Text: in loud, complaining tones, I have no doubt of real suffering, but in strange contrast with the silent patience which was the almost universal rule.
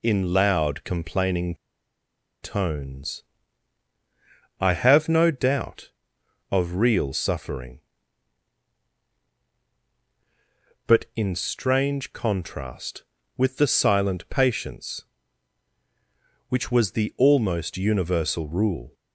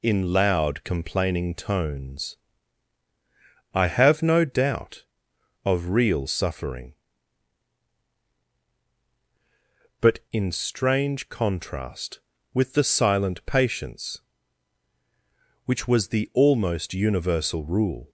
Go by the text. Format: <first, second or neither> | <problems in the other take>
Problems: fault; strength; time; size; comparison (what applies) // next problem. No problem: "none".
second | pauses between "complaining" and "tones"; noticeable; at 1.5 s; 0.88 s long